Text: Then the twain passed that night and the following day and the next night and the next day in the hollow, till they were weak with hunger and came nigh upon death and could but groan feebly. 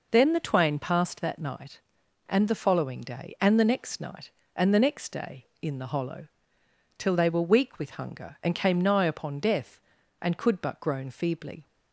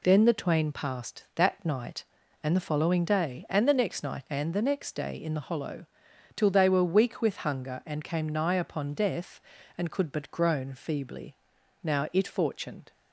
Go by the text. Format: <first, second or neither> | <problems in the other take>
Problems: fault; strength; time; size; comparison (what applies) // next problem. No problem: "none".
first | goes on to say "Now it fortuned"; noticeable; from 11.8 s on; 1.1 s long